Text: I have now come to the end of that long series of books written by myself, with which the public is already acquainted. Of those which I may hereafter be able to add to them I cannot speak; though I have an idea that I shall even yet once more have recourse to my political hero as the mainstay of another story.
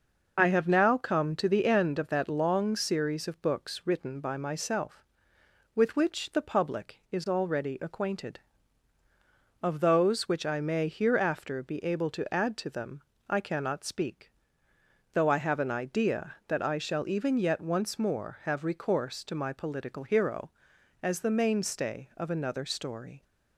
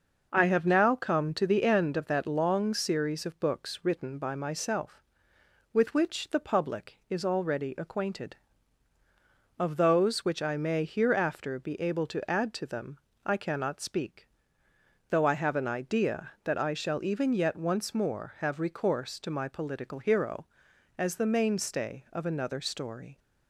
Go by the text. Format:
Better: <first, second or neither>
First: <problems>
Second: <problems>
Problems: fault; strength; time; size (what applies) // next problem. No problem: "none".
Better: second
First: loses the start of "I"; at 0.3 s; 45 ms // pauses between "them" and "I"; slight; at 13.0 s; 0.26 s long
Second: pauses between "them" and "I"; slight; at 12.9 s; 0.26 s long